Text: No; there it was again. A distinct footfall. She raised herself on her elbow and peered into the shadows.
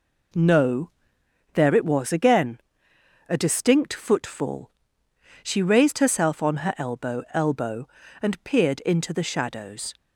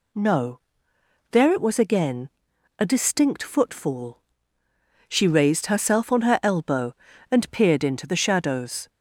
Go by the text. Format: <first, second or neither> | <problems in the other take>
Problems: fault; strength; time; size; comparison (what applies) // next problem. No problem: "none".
second | says "elbow" twice; at 7.3 s